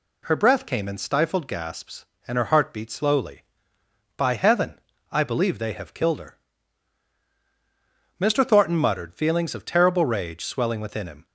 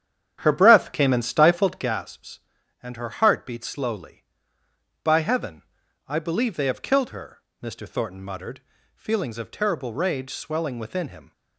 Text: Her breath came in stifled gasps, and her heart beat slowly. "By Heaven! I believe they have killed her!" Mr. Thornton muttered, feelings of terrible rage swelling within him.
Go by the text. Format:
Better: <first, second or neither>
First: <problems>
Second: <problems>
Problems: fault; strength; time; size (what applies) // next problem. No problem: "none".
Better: first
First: none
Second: starts louder than the rest; strong; until 2.0 s; 9 dB